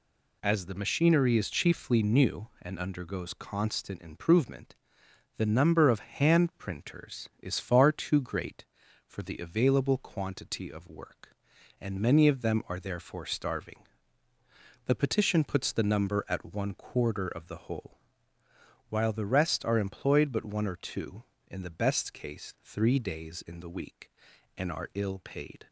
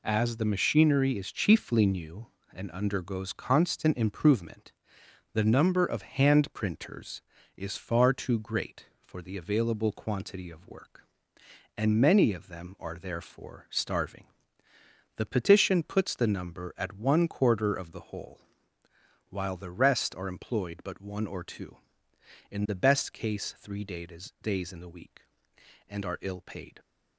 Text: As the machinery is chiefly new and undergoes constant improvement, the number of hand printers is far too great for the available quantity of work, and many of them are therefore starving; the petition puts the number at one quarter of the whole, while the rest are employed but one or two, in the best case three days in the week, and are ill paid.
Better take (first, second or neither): first